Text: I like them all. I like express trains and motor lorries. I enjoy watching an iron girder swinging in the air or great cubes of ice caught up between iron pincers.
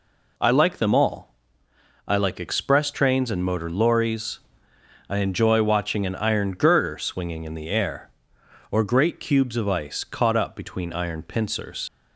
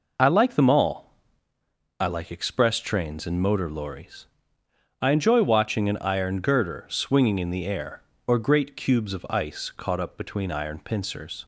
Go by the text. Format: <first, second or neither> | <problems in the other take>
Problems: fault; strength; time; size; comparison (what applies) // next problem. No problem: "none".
second | leaves "pincers" unfinished; at 11.8 s; 115 ms